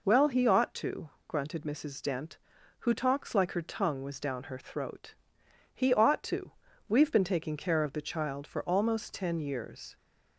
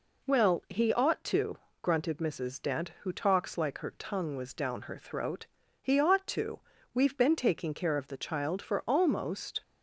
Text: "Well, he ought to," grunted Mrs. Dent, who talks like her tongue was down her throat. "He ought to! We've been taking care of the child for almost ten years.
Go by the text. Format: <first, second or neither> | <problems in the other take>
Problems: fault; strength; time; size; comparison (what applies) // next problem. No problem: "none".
first | stops before "ten years"; at 9.6 s